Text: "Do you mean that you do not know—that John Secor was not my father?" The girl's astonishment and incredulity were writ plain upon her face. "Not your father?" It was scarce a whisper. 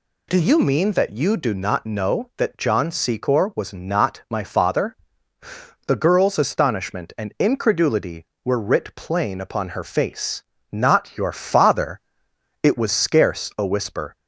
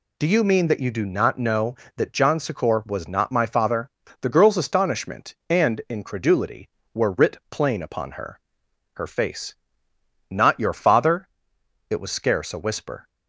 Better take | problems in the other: first | says "her" twice; at 8.9 s

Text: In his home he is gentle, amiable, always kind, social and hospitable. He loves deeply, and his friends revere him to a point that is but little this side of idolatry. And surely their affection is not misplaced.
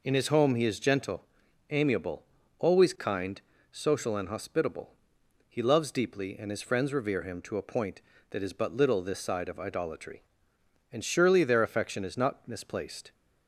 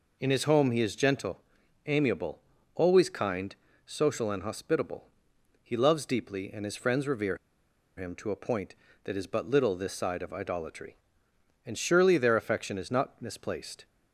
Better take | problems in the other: first | pauses between "revere" and "him"; noticeable; at 7.3 s; 0.61 s long

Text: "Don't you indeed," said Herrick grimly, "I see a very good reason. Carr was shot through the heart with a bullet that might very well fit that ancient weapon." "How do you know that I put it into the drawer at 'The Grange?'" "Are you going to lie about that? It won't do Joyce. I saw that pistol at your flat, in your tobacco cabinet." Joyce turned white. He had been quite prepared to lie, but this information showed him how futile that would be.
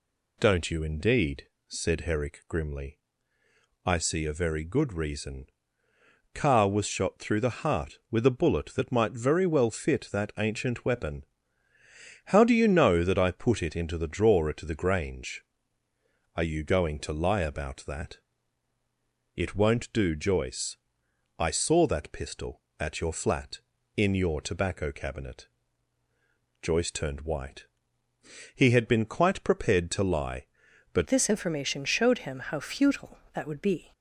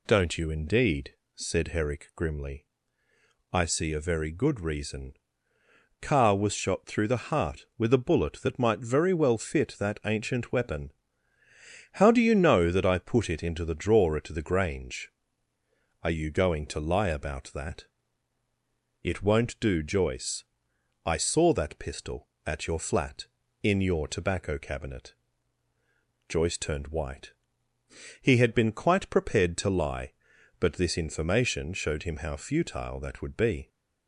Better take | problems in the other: second | changes voice at "this"; from 31.0 s on; 2.9 s long

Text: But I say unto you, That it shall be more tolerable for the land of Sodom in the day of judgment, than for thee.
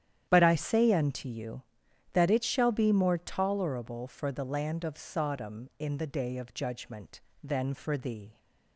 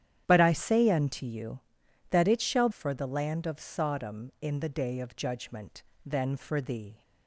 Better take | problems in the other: first | starts louder than the rest; strong; until 1.2 s; 10.5 dB; strong in the first // skips "be more tolerable"; at 2.6 s

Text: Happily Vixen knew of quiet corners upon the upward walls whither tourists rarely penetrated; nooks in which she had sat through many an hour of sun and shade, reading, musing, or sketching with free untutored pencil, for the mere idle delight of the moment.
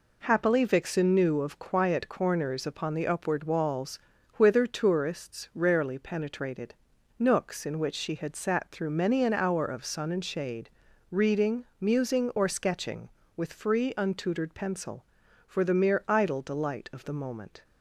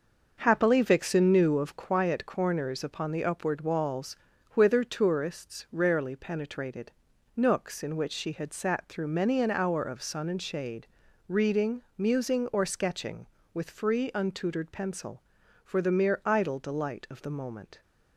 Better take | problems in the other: first | starts louder than the rest; until 2.0 s; 6.5 dB // pauses between "walls" and "whither"; at 4.1 s; 0.38 s long; also in the first

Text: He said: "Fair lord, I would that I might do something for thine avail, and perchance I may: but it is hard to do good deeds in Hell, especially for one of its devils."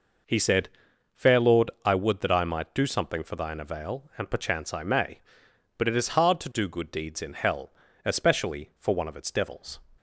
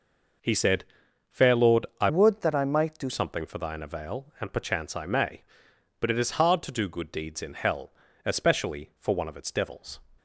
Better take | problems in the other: first | changes voice from "would" to "do"; from 2.0 to 3.0 s; 1.0 s long

